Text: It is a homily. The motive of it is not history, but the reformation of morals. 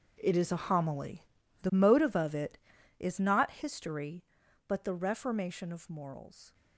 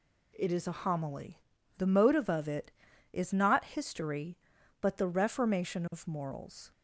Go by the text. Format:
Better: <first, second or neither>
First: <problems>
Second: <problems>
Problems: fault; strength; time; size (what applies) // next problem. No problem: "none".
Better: second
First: gets quieter; strong; throughout; 13.5 dB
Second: none